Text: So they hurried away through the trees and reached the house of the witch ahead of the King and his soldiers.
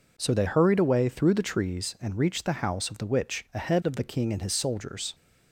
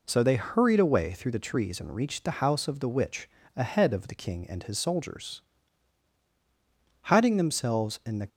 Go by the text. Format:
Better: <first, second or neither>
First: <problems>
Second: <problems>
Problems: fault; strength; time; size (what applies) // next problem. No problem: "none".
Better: first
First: none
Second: pauses between "witch" and "ahead"; slight; at 3.2 s; 0.26 s long // goes on to say "Hiding themselves in the"; noticeable; from 7.0 s on; 1.2 s long